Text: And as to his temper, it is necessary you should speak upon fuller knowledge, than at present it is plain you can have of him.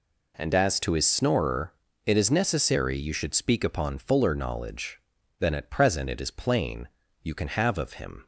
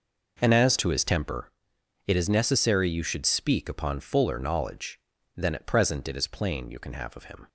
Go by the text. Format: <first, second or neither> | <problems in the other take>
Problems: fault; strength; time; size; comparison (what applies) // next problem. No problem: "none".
second | says "snorer" for "temper"; at 1.0 s // pauses between "plain" and "you"; slight; at 6.8 s; 0.36 s long